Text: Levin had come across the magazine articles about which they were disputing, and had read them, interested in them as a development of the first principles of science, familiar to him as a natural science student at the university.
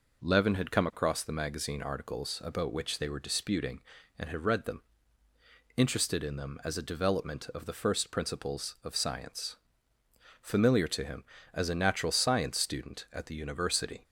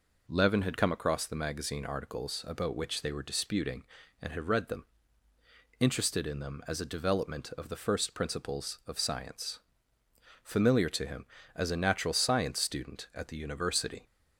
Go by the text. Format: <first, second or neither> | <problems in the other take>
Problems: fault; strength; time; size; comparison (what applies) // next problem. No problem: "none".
neither | none